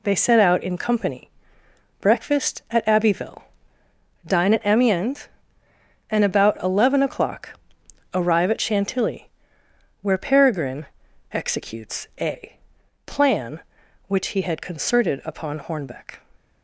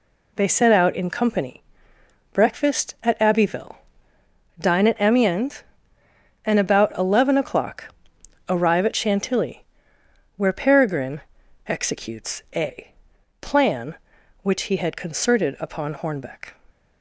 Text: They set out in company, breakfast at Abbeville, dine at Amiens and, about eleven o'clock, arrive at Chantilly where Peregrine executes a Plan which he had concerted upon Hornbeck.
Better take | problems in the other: neither | pauses between "Chantilly" and "where"; noticeable; the same in both // pauses between "Peregrine" and "executes"; noticeable; the same in both // pauses between "a" and "Plan"; noticeable; the same in both

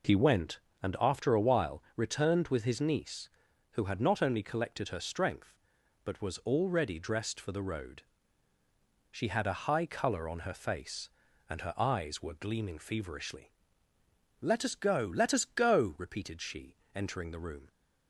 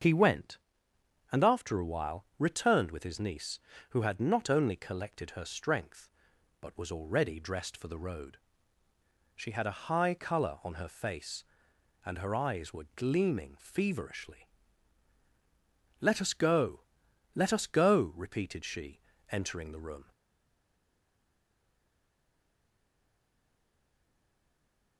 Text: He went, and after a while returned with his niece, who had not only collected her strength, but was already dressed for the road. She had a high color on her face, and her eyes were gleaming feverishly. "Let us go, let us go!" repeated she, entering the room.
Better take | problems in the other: first | starts louder than the rest; until 1.7 s; 7 dB // stays silent after the last word; strong; from 20.1 s on; 4.8 s long

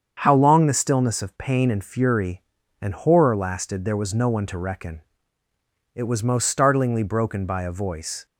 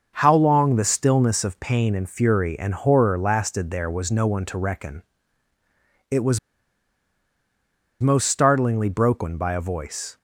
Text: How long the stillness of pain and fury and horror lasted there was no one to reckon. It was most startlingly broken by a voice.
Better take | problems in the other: first | starts louder than the rest; until 1.1 s; 6.5 dB; strong in the first // pauses between "was" and "most"; strong; at 6.3 s; 1.6 s long

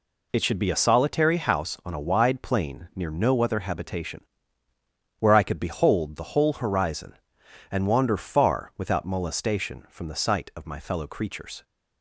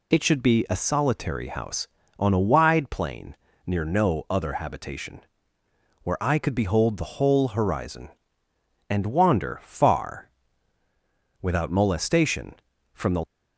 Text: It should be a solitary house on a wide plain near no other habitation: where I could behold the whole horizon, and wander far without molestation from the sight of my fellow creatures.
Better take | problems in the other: first | pauses between "plain" and "near"; slight; at 3.3 s; 0.32 s long // pauses between "far" and "without"; at 10.2 s; 1.1 s long // stops before "sight of my fellow creatures"; at 13.2 s

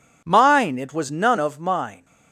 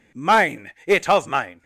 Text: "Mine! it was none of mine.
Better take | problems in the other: first | skips "was none"; at 1.0 s

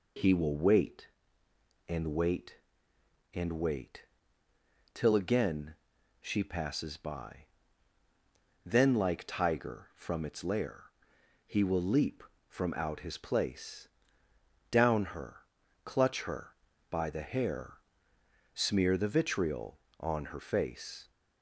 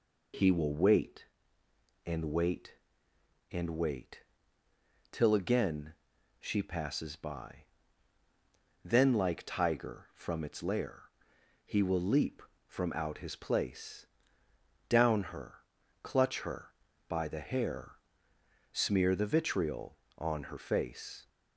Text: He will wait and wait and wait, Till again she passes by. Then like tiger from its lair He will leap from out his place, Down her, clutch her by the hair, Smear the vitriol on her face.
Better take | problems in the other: neither | pauses between "again" and "she"; noticeable; the same in both // pauses between "lair" and "He"; noticeable; the same in both

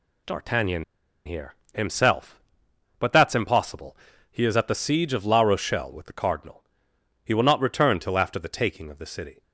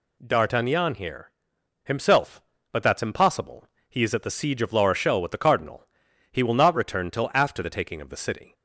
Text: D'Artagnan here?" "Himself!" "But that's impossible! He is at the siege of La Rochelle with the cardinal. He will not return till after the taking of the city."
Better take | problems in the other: second | pauses between "D'Artagnan" and "here"; at 0.8 s; 0.41 s long

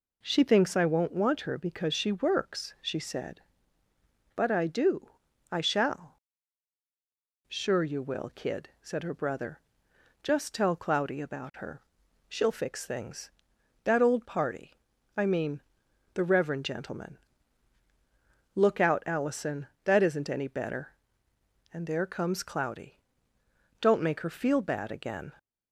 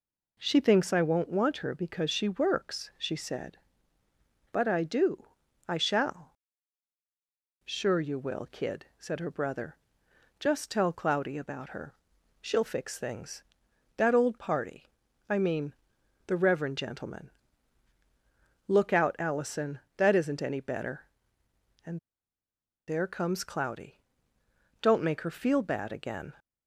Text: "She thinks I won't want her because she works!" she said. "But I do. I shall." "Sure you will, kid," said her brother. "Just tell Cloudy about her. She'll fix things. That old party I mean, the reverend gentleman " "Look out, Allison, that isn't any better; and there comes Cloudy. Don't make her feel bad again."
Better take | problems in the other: first | pauses between "party" and "I"; at 14.8 s; 0.42 s long; also in the first // pauses between "and" and "there"; noticeable; at 21.9 s; 0.90 s long

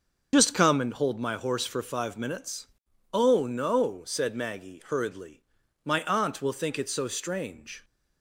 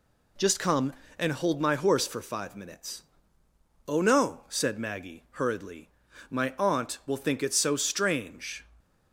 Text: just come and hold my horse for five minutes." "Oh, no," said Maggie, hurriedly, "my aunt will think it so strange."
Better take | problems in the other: second | loses the start of "just"; at 0.3 s; 50 ms // starts louder than the rest; until 1.3 s; 6.5 dB

